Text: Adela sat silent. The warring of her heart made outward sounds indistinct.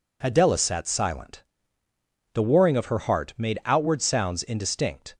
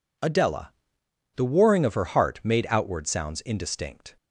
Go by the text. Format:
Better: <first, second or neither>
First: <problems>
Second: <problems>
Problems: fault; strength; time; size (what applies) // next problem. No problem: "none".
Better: first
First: none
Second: skips "sat silent"; at 1.0 s